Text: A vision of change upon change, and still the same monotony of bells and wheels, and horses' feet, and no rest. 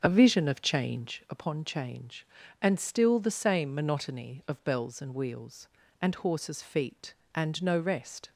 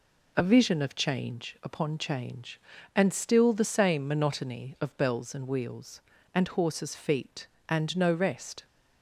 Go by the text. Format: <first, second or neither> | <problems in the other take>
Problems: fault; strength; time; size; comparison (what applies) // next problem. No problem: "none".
second | starts louder than the rest; noticeable; until 1.4 s; 6 dB